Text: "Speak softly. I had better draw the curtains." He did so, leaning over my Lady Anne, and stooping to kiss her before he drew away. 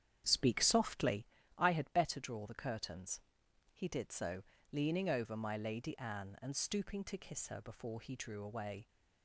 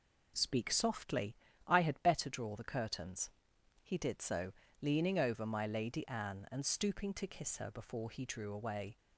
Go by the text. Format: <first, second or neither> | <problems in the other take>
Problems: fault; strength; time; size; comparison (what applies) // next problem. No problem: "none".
second | starts louder than the rest; strong; until 1.3 s; 9 dB